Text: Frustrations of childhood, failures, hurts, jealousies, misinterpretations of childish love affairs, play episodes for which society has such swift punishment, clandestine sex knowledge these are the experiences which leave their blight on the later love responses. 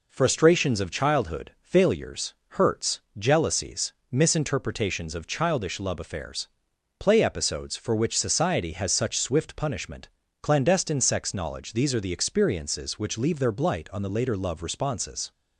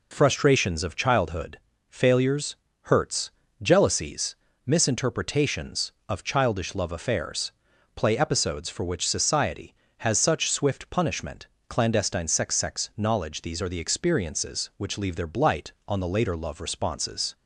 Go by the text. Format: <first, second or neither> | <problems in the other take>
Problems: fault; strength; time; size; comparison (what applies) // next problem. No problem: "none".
first | says "sex" twice; at 12.5 s